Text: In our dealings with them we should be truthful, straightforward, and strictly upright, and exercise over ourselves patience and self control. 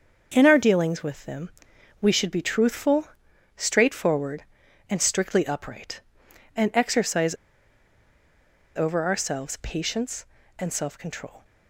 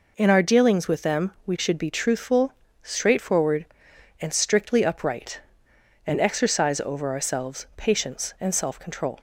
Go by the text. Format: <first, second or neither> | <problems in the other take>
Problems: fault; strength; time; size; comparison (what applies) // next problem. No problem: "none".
second | starts louder than the rest; until 1.3 s; 6.5 dB // pauses between "them" and "we"; noticeable; at 1.5 s; 0.50 s long // pauses between "exercise" and "over"; strong; at 7.3 s; 1.4 s long